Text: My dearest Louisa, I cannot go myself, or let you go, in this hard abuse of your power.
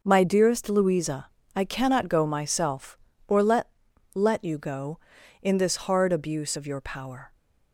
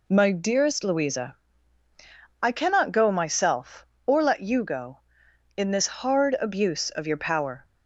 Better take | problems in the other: second | says "let" twice; at 4.1 s

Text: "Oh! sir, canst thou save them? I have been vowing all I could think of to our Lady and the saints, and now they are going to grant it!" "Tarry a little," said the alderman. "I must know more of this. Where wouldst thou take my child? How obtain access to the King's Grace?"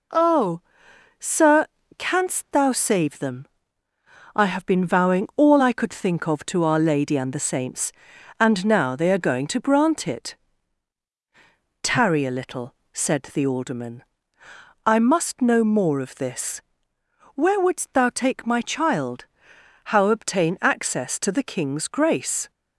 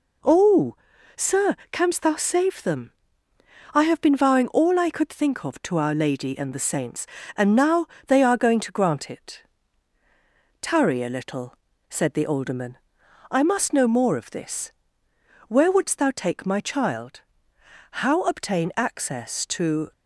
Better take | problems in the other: first | pauses between "now" and "they"; slight; at 7.8 s; 0.22 s long // stops before "the King's Grace"; at 19.9 s

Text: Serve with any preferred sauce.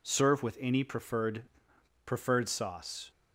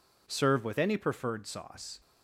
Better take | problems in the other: second | says "preferred" twice; at 2.0 s

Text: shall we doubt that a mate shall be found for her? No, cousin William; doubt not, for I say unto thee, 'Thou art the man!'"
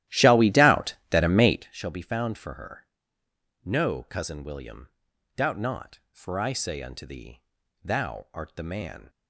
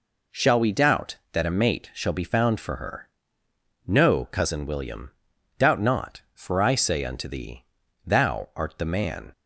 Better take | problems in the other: second | starts louder than the rest; strong; until 1.7 s; 14 dB

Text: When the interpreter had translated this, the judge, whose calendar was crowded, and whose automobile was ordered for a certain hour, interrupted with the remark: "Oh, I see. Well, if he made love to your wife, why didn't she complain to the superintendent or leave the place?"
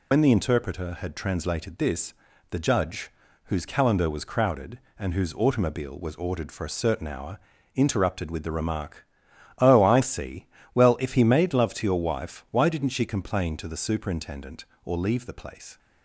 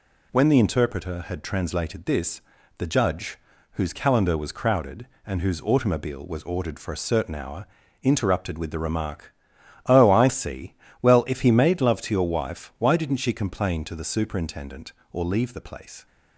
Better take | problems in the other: second | loses the start of "When"; at 0.1 s; 70 ms

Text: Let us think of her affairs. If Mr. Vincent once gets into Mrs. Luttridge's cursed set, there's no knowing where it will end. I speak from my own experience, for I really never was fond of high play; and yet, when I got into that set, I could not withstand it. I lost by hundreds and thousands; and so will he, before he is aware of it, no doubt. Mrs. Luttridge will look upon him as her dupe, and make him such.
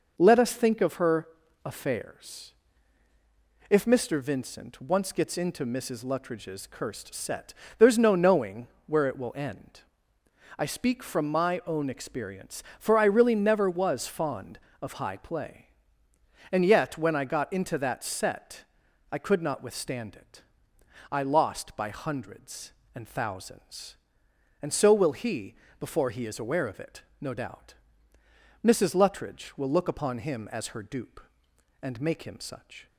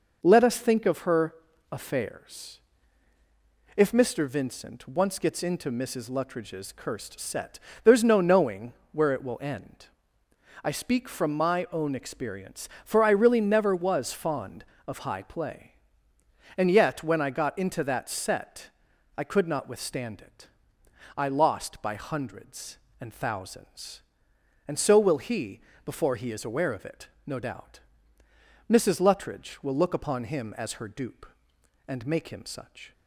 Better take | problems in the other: neither | pauses between "her" and "affairs"; the same in both // pauses between "knowing" and "where"; slight; the same in both

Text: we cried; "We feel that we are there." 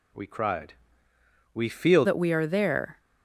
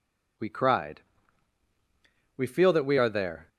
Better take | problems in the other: second | changes voice at "that"; from 2.0 s on; 0.9 s long

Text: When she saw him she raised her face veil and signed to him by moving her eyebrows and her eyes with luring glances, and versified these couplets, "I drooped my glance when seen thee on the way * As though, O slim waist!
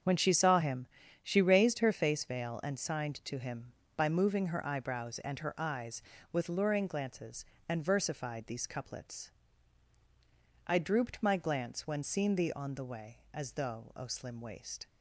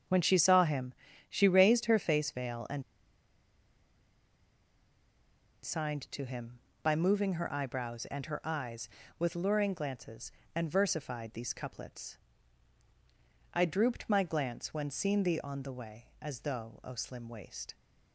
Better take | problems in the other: first | starts louder than the rest; until 1.4 s; 7 dB; strong in the first // pauses between "him" and "she"; slight; at 0.9 s; 0.34 s long; slight in the first // pauses between "and" and "signed"; strong; at 2.8 s; 2.8 s long

